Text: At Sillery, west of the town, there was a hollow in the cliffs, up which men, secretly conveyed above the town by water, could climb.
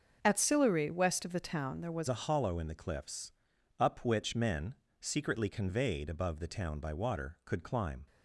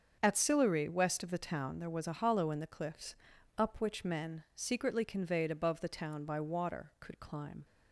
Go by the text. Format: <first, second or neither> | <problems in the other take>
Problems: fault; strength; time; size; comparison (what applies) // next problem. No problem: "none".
second | starts louder than the rest; until 1.2 s; 6.5 dB; also in the second // changes voice at "a"; from 2.0 s on; 6.0 s long